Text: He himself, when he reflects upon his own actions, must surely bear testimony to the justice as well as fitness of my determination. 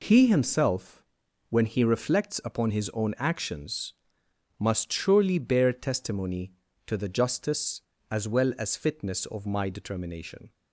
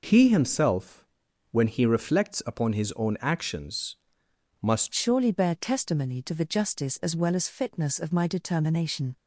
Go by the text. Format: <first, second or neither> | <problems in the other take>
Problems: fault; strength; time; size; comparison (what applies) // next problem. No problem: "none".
first | changes voice at "surely"; from 4.9 s on; 4.2 s long